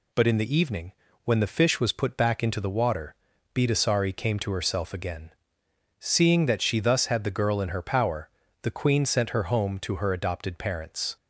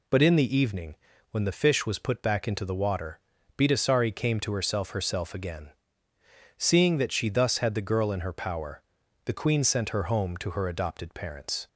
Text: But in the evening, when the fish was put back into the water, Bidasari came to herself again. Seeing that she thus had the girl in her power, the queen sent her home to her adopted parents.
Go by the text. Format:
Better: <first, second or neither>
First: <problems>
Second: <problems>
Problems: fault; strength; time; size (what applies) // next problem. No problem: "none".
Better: first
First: none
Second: says "herself" twice; at 4.9 s